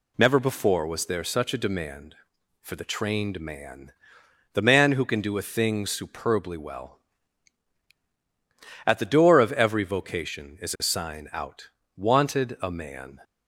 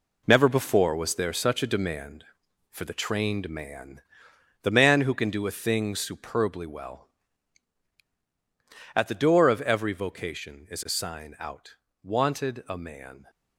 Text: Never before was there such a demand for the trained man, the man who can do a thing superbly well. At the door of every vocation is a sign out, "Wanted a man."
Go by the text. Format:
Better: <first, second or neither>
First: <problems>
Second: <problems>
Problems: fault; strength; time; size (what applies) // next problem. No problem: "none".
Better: first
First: none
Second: gets quieter; strong; throughout; 8.5 dB